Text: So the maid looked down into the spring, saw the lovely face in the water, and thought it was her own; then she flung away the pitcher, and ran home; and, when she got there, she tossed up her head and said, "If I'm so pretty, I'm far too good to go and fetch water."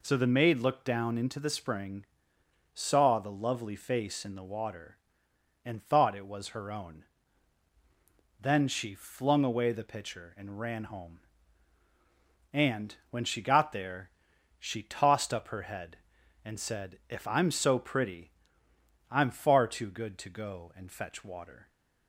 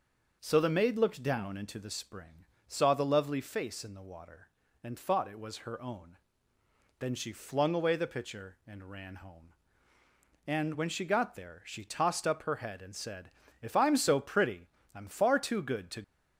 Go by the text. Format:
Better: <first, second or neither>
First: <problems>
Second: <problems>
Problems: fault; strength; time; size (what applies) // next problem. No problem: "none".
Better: first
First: none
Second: starts louder than the rest; noticeable; until 1.4 s; 6 dB // stops before "go and fetch water"; at 16.0 s